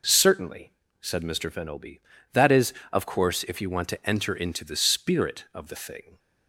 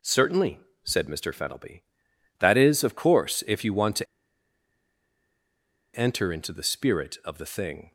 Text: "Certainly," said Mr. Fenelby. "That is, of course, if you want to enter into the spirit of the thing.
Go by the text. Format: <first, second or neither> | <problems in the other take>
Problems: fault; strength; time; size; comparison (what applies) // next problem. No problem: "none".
first | pauses between "to" and "enter"; strong; at 4.0 s; 1.9 s long